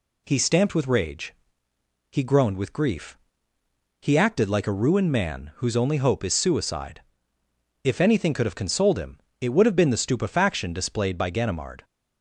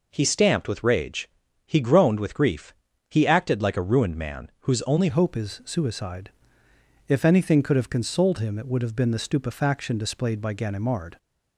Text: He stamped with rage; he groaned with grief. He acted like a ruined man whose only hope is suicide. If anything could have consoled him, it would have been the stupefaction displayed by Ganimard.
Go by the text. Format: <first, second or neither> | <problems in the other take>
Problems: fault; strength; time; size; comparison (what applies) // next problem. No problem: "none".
first | changes voice at "hope"; from 5.0 s on; 6.1 s long